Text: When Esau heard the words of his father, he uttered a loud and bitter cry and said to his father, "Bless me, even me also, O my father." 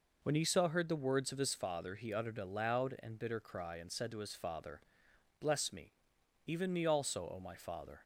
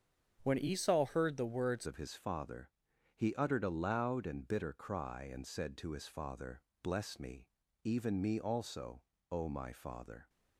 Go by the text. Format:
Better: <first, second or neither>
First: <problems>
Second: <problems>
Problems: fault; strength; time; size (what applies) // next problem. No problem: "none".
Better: first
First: none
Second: starts louder than the rest; strong; until 1.4 s; 7.5 dB // changes voice at "of"; from 1.8 s on; 8.4 s long